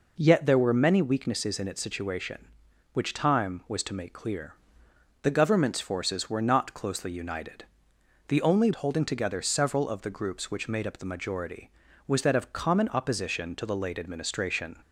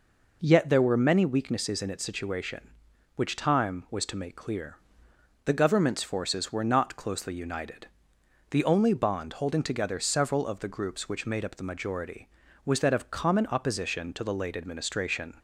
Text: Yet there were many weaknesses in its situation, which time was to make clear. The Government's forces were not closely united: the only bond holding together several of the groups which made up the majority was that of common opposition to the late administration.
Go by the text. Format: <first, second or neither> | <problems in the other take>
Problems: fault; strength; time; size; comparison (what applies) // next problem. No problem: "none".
second | skips "bond"; at 8.7 s